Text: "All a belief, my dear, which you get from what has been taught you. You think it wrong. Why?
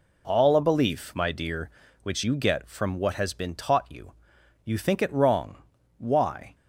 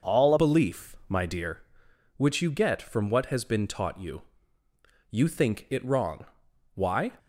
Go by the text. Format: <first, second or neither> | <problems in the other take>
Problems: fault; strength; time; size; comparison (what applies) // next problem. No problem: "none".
first | changes voice at "belief"; from 0.3 s on; 6.8 s long